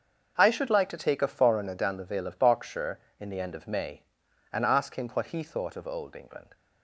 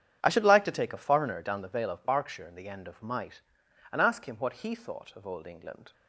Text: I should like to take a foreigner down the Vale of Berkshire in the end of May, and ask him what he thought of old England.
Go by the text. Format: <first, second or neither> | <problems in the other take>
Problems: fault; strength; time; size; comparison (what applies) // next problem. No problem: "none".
first | starts louder than the rest; strong; until 1.2 s; 9 dB; also in the first // says "Might" for "May"; at 3.0 s